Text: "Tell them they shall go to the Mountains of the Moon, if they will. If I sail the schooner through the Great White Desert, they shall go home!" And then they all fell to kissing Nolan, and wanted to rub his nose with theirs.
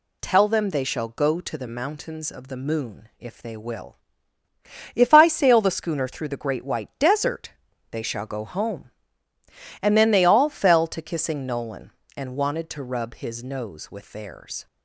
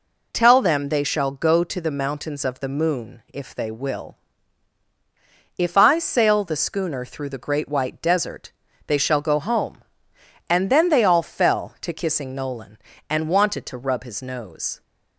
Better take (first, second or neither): first